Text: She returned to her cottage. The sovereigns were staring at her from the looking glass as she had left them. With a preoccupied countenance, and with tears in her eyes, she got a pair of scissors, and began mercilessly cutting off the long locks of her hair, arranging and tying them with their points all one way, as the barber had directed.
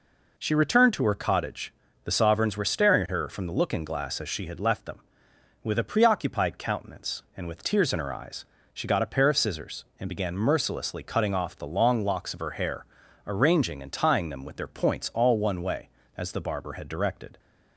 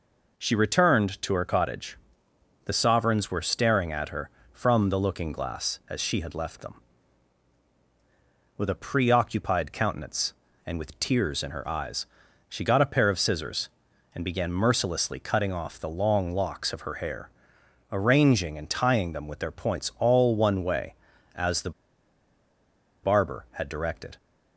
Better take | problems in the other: first | pauses between "the" and "barber"; strong; at 21.7 s; 1.3 s long

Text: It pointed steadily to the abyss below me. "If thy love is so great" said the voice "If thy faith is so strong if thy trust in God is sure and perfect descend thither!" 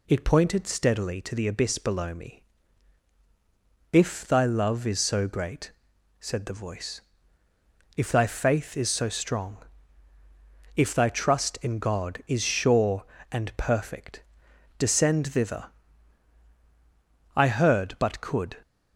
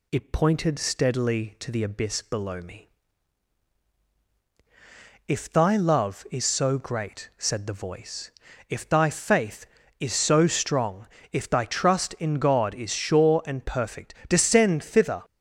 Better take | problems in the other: second | pauses between "great" and "said"; noticeable; at 5.7 s; 0.48 s long // pauses between "voice" and "If"; noticeable; at 6.9 s; 0.96 s long; also in the second // pauses between "strong" and "if"; at 9.6 s; 1.1 s long; slight in the second // pauses between "perfect" and "descend"; noticeable; at 14.2 s; 0.54 s long; slight in the second // goes on to say "I heard but could"; noticeable; from 17.3 s on; 1.2 s long

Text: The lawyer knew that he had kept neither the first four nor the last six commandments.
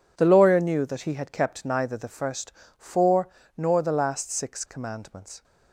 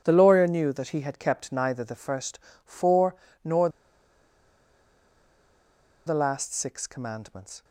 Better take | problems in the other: first | pauses between "first" and "four"; slight; at 2.3 s; 0.26 s long; slight in the first // pauses between "four" and "nor"; slight; at 3.1 s; 0.28 s long; slight in the first // pauses between "nor" and "the"; strong; at 3.6 s; 2.3 s long

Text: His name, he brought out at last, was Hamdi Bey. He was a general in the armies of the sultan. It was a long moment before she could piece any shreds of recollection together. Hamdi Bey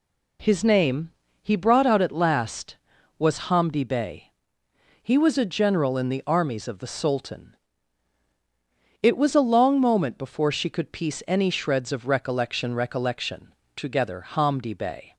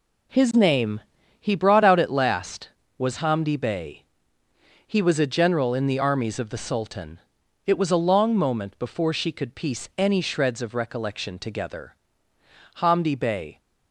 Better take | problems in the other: second | says "recollection" twice; at 12.7 s

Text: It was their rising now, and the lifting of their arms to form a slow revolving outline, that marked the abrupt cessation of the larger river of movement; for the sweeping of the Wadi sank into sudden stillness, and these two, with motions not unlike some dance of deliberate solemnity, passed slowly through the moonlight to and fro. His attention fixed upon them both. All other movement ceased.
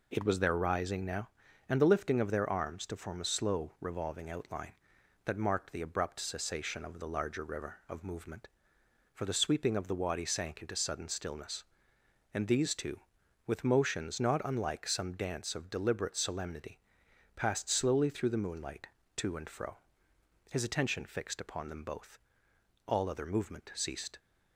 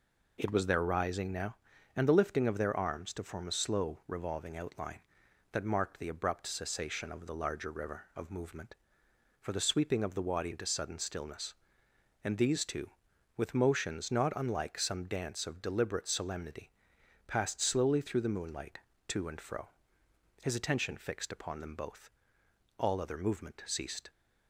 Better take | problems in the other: first | skips "sank"; at 10.5 s

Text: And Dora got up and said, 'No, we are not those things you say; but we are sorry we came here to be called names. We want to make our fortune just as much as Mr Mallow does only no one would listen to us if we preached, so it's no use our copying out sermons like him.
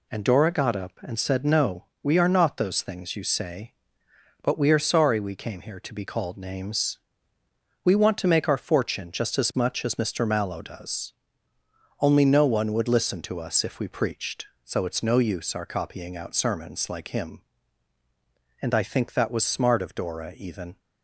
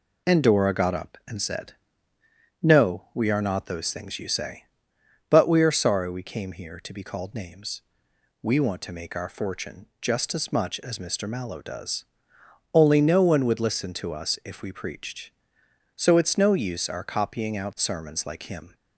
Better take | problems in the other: second | pauses between "does" and "only"; noticeable; at 11.1 s; 0.88 s long; noticeable in the second // goes on to say "And I think that was smart of Dora even"; strong; from 18.6 s on; 2.1 s long

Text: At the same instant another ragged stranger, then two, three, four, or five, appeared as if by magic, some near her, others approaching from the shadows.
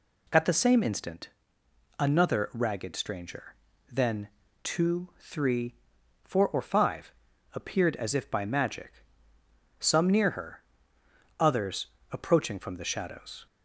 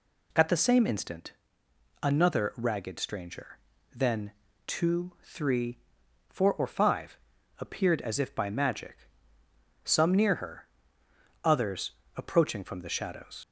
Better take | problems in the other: first | pauses between "instant" and "another"; noticeable; at 1.3 s; 0.70 s long; noticeable in the first // pauses between "then" and "two"; slight; at 4.3 s; 0.34 s long; slight in the first // pauses between "others" and "approaching"; slight; at 11.9 s; 0.26 s long; slight in the first // leaves "shadows" unfinished; at 13.4 s; 70 ms

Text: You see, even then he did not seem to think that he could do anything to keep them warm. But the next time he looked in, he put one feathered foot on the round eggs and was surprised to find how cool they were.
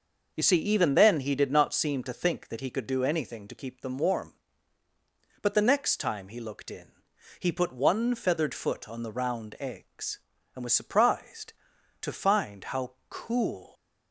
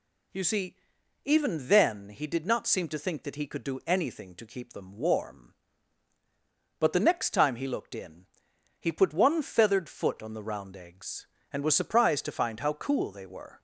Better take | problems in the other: second | pauses between "how" and "cool"; slight; at 12.9 s; 0.18 s long // stops before "they were"; at 13.7 s

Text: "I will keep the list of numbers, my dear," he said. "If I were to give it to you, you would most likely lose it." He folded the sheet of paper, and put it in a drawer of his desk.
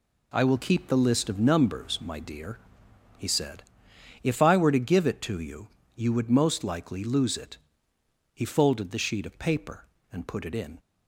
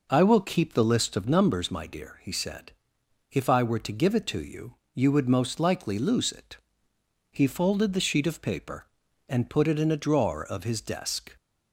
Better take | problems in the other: second | stops before "a drawer of his desk"; at 10.7 s

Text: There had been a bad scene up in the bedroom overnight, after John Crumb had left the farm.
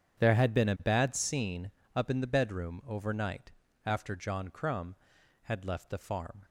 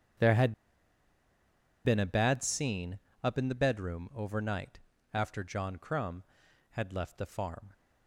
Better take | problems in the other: first | starts louder than the rest; strong; until 2.5 s; 8.5 dB; strong in the first // pauses between "had" and "been"; strong; at 0.5 s; 1.3 s long // pauses between "scene" and "up"; slight; at 2.9 s; 0.24 s long; slight in the first

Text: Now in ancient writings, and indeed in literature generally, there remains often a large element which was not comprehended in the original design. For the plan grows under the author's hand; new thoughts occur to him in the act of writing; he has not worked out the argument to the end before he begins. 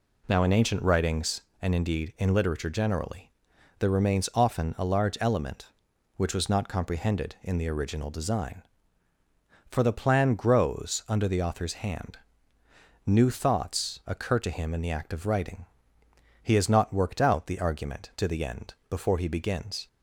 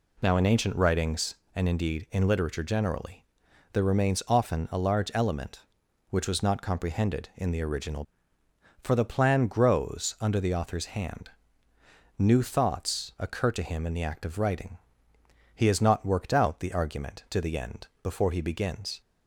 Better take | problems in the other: first | skips "design"; at 8.4 s

